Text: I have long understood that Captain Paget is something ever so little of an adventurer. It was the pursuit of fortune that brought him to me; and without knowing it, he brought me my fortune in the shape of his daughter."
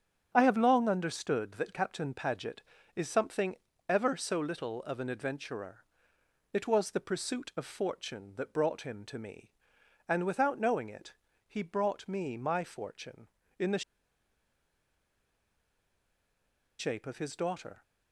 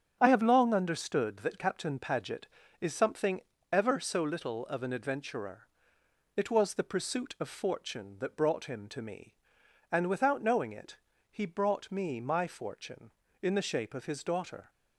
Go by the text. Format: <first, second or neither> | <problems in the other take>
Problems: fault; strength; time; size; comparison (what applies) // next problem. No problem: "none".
second | starts louder than the rest; strong; until 1.3 s; 8 dB; strong in the second // pauses between "something" and "ever"; slight; at 3.5 s; 0.32 s long; slight in the second // pauses between "the" and "shape"; strong; at 13.8 s; 2.9 s long